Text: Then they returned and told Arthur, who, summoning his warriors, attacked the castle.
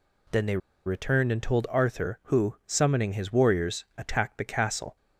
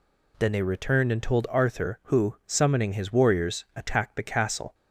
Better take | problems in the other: second | pauses between "they" and "returned"; slight; at 0.5 s; 0.27 s long

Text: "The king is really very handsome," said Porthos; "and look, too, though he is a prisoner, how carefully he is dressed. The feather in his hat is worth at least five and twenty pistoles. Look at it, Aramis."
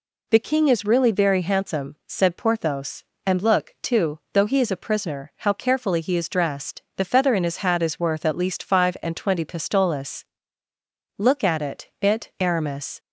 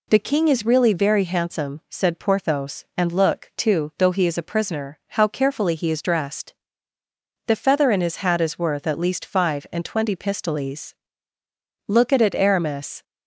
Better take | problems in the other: second | says "it" twice; at 12.0 s

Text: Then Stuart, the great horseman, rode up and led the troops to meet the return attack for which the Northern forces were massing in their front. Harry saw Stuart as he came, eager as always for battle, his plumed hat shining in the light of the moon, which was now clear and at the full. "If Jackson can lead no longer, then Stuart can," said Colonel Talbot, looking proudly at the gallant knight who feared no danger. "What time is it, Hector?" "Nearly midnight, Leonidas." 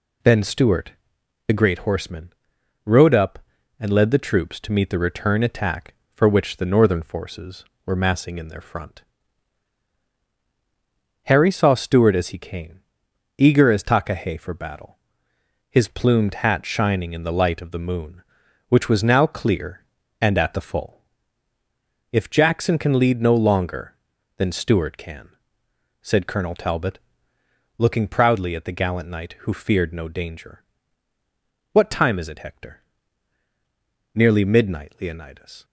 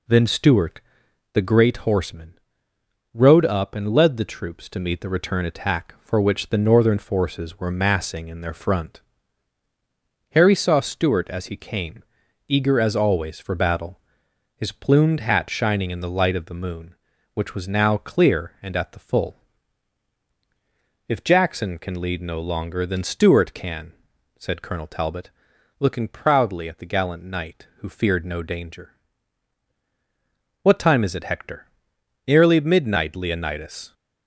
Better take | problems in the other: second | says "takahe" for "always"; at 13.8 s

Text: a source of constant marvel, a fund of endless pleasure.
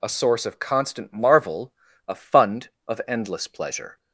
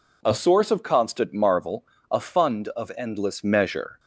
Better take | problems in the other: first | says "measure" for "pleasure"; at 3.4 s

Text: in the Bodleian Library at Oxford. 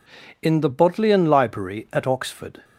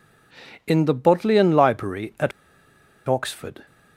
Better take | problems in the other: first | pauses between "at" and "Oxford"; noticeable; at 2.3 s; 0.76 s long

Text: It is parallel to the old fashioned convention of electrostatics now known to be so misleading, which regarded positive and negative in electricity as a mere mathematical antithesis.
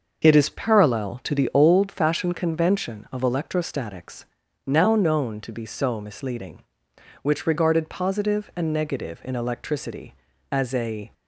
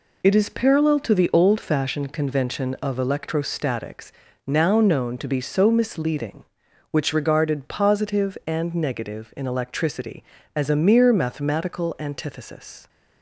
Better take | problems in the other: second | starts louder than the rest; until 1.2 s; 6 dB // pauses between "electrostatics" and "now"; at 4.2 s; 0.40 s long; also in the second // stops before "mere mathematical antithesis"; at 11.1 s

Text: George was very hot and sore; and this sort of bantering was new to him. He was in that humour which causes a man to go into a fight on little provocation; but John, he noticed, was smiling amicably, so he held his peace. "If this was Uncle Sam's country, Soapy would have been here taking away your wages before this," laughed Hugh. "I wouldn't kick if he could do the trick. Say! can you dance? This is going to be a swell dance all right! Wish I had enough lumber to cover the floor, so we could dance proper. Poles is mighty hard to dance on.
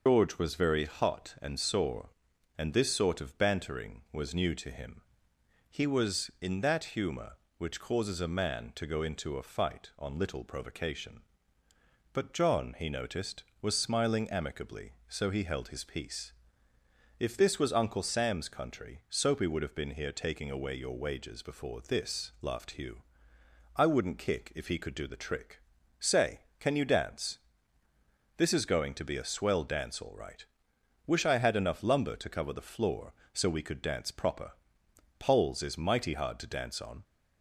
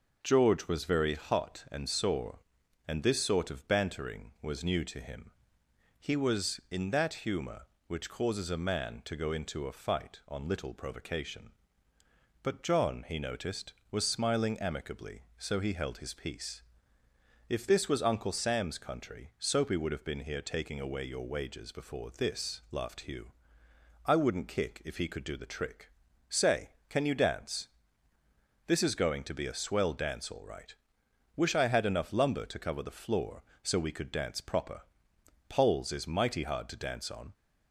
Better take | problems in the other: second | loses the start of "George"; at 0.0 s; 130 ms

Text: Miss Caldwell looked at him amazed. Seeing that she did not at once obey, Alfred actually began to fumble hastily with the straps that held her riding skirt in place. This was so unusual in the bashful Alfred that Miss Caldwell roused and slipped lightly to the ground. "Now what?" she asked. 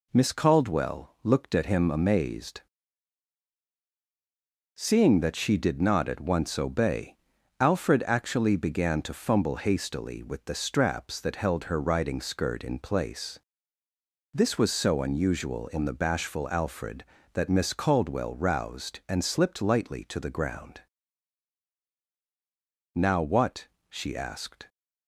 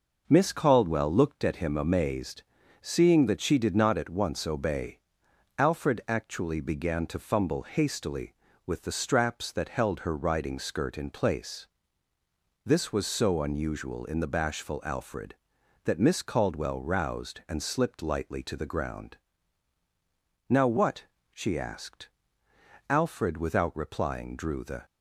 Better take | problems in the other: first | goes on to say "Alfred without replying drew the"; strong; from 22.8 s on; 1.9 s long

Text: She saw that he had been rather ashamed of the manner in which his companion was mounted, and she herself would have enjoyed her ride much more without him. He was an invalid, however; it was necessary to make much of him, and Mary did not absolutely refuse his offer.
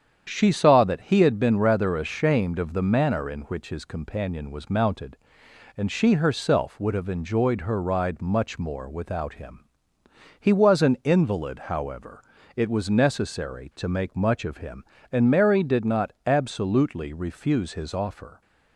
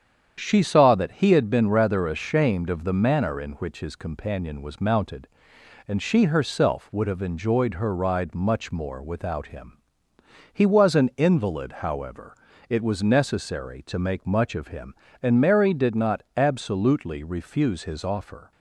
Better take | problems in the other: neither | starts louder than the rest; strong; the same in both

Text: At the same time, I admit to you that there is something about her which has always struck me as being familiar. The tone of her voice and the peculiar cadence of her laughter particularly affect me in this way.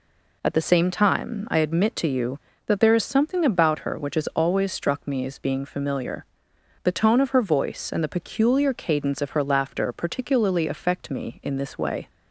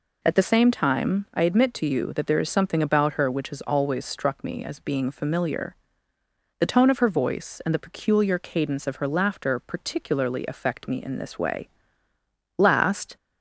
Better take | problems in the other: first | goes on to say "Last"; from 12.5 s on; 0.58 s long

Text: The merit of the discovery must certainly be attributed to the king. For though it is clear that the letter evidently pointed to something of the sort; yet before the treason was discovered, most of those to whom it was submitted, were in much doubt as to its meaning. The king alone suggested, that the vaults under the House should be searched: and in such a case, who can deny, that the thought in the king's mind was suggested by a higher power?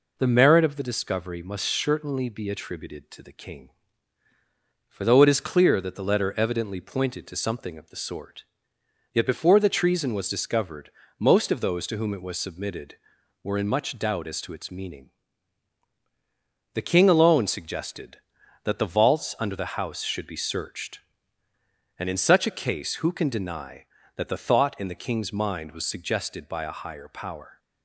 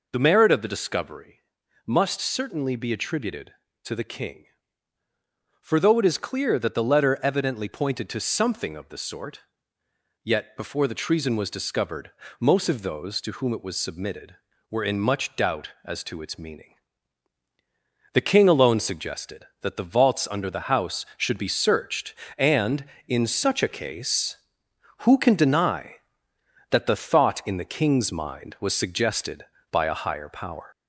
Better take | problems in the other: first | gets louder; slight; throughout; 3.5 dB // pauses between "discovery" and "must"; at 1.4 s; 0.42 s long

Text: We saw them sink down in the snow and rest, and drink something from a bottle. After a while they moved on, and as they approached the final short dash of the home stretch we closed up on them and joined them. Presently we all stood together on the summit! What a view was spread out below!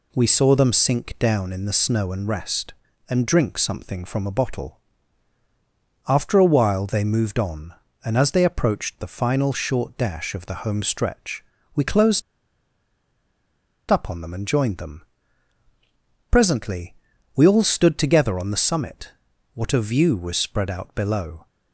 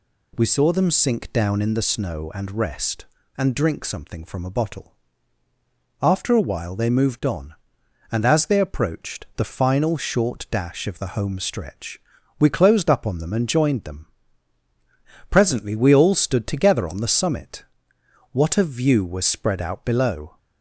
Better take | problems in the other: second | pauses between "stretch" and "we"; slight; at 11.4 s; 0.30 s long; also in the second // pauses between "closed" and "up"; strong; at 12.2 s; 1.6 s long // pauses between "Presently" and "we"; at 16.9 s; 0.40 s long

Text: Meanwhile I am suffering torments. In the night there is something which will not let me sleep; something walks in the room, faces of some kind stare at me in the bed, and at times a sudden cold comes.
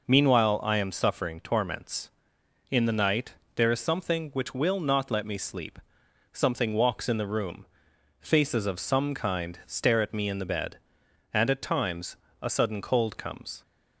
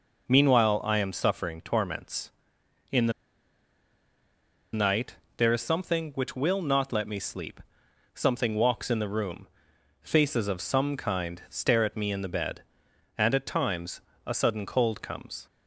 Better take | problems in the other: first | pauses between "the" and "night"; strong; at 3.1 s; 1.6 s long // pauses between "night" and "there"; slight; at 5.1 s; 0.20 s long; slight in the first // pauses between "times" and "a"; slight; at 13.9 s; 0.26 s long; slight in the first

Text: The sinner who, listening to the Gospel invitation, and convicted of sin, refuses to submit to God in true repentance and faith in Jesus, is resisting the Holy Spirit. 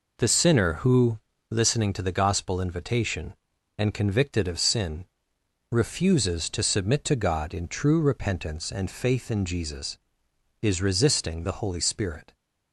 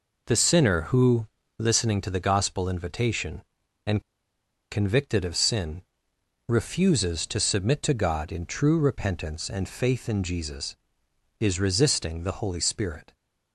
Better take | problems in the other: first | pauses between "and" and "convicted"; noticeable; at 4.0 s; 0.70 s long

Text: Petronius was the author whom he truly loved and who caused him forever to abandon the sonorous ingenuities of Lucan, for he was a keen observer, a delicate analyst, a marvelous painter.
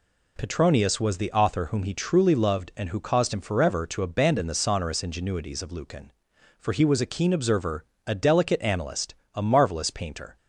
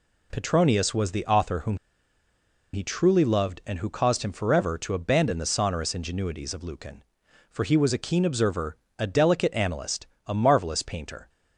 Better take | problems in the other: first | pauses between "whom" and "he"; at 1.7 s; 0.98 s long

